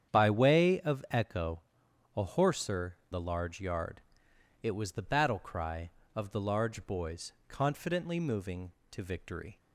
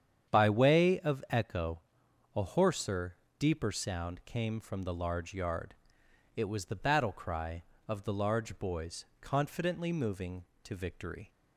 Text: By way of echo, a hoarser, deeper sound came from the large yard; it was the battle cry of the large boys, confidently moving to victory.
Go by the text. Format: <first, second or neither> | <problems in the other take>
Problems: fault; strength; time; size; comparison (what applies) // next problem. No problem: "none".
second | starts louder than the rest; strong; until 1.1 s; 8.5 dB; strong in the second // skips "deeper sound came from"; at 3.0 s